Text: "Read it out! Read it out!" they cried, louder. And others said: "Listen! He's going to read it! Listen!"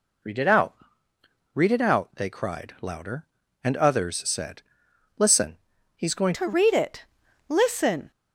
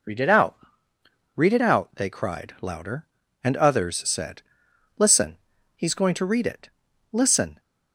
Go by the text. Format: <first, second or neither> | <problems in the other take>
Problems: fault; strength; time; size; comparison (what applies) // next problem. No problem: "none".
second | changes voice at "to"; from 6.3 s on; 1.8 s long